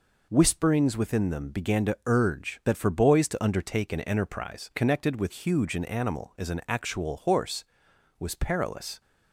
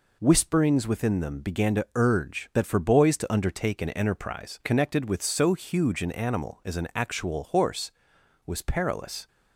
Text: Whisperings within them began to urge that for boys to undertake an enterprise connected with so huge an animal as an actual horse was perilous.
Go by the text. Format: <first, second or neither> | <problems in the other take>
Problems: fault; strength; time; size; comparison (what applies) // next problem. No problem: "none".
second | skips "so"; at 5.3 s